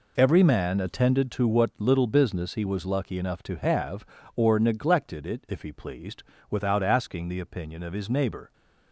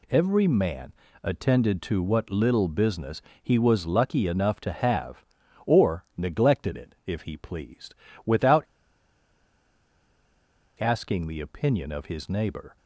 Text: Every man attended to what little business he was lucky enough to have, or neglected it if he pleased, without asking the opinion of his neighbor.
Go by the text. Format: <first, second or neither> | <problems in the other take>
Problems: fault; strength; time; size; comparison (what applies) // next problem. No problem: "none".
first | pauses between "man" and "attended"; slight; at 0.9 s; 0.30 s long // pauses between "business" and "he"; slight; at 3.2 s; 0.20 s long // pauses between "without" and "asking"; strong; at 8.6 s; 2.1 s long